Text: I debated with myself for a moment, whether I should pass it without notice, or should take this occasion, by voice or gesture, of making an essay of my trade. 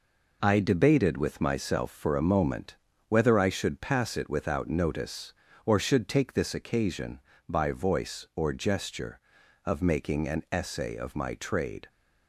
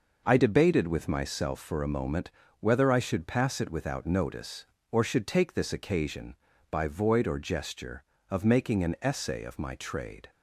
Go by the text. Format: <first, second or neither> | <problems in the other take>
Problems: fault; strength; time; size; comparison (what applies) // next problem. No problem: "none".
first | says "void" for "voice"; at 6.8 s